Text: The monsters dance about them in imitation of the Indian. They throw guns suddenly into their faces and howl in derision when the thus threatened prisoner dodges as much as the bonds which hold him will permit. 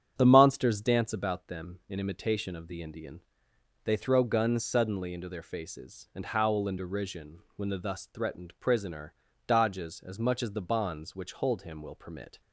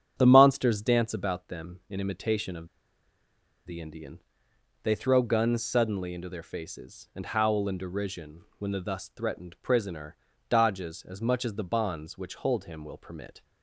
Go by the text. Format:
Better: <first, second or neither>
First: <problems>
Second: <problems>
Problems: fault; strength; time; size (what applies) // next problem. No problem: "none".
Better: first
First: starts louder than the rest; strong; until 1.1 s; 8 dB // pauses between "derision" and "when"; slight; at 7.3 s; 0.18 s long // pauses between "prisoner" and "dodges"; slight; at 9.1 s; 0.32 s long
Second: starts louder than the rest; strong; until 1.1 s; 8 dB // pauses between "of" and "the"; at 2.6 s; 0.98 s long // pauses between "derision" and "when"; slight; at 8.4 s; 0.18 s long // pauses between "prisoner" and "dodges"; slight; at 10.1 s; 0.32 s long